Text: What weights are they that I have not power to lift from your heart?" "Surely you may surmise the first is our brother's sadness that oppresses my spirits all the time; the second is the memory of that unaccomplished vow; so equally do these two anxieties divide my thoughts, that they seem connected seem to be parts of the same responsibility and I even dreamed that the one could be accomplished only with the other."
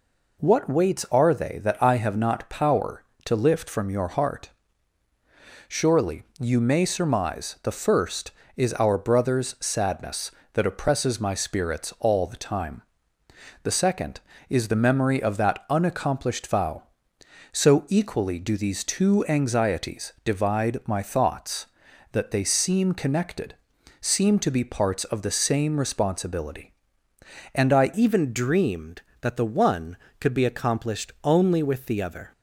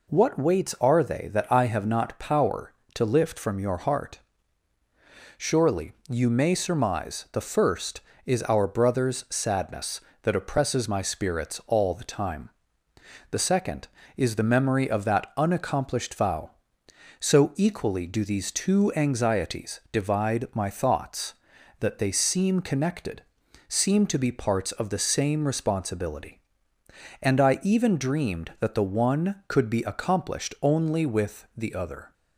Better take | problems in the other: second | pauses between "Surely" and "you"; slight; at 6.2 s; 0.16 s long; slight in the second // pauses between "connected" and "seem"; at 23.5 s; 0.44 s long; also in the second // changes voice at "even"; from 27.9 s on; 4.4 s long

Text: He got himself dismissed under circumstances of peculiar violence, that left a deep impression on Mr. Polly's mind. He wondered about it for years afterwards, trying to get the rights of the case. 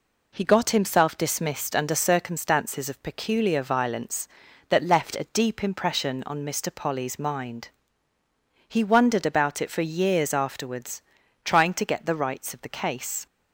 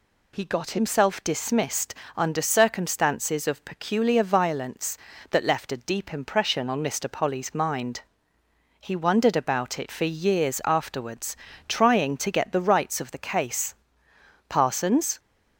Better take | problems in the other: first | pauses between "dismissed" and "under"; slight; at 1.9 s; 0.22 s long // goes on to say "Parsons"; noticeable; from 14.4 s on; 0.70 s long

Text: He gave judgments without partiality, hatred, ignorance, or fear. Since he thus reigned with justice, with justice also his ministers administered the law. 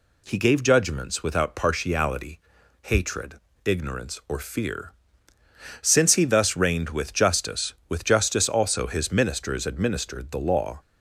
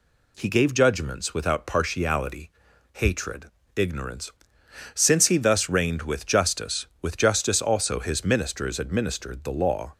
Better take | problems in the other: first | skips "or fear"; at 4.6 s

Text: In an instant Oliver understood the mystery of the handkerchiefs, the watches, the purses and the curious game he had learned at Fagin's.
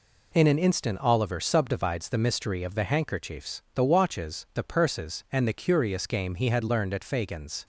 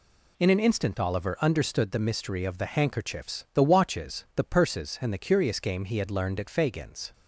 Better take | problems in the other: second | says "subdivides" for "understood"; at 1.3 s

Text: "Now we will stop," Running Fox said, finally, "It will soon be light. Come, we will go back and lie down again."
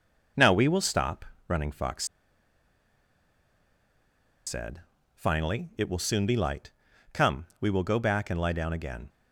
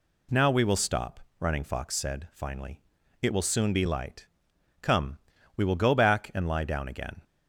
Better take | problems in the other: second | pauses between "Fox" and "said"; strong; at 2.0 s; 2.4 s long

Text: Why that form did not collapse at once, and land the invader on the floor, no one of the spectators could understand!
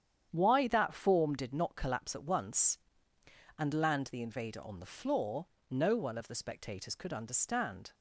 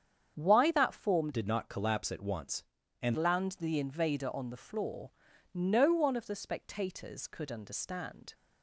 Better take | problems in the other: first | starts louder than the rest; strong; until 1.3 s; 8 dB; strong in the first // changes voice from "did" to "and"; from 1.3 to 3.1 s; 1.8 s long

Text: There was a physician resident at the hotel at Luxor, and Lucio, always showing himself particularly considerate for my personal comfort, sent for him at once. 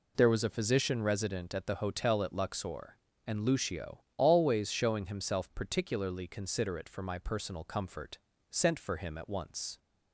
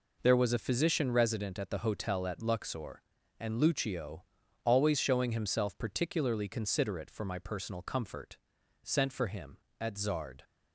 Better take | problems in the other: first | says "zard" for "once"; at 9.9 s

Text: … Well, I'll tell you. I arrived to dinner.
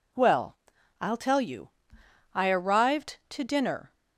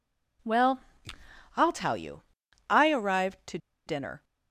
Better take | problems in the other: first | pauses between "to" and "dinner"; slight; at 3.5 s; 0.29 s long

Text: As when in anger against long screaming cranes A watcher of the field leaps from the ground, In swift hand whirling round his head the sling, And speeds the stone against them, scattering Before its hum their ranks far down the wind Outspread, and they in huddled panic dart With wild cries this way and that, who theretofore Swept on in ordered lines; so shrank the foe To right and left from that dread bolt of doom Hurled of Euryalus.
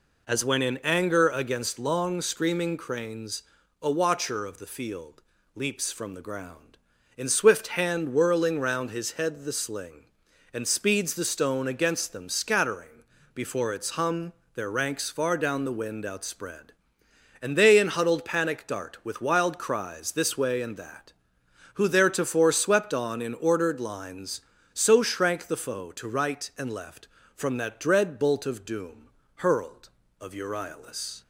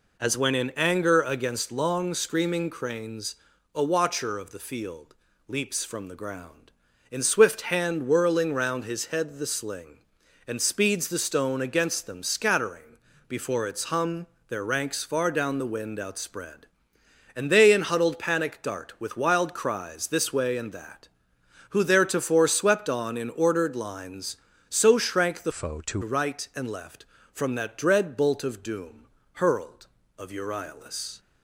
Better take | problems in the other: first | pauses between "cranes" and "A"; at 3.3 s; 0.38 s long; also in the first // pauses between "field" and "leaps"; slight; at 5.1 s; 0.34 s long; slight in the first // pauses between "scattering" and "Before"; slight; at 12.9 s; 0.30 s long; slight in the first // pauses between "hum" and "their"; slight; at 14.2 s; 0.22 s long; slight in the first // changes voice from "foe" to "To"; from 25.5 to 26.0 s; 0.5 s long // pauses between "doom" and "Hurled"; slight; at 29.0 s; 0.30 s long; slight in the first

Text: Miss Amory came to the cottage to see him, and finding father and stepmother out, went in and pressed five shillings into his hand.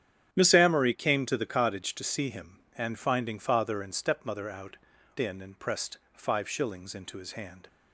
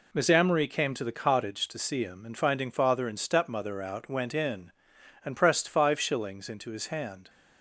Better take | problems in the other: second | starts louder than the rest; strong; until 1.3 s; 9.5 dB // skips "went"; at 4.9 s // pauses between "pressed" and "five"; slight; at 5.9 s; 0.16 s long

